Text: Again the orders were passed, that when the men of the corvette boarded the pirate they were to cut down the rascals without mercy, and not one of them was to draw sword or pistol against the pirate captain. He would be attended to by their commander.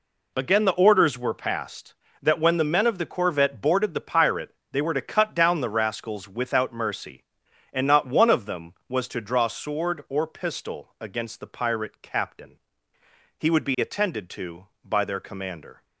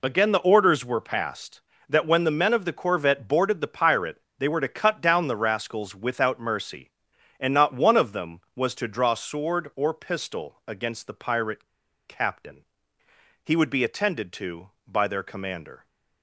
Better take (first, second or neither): first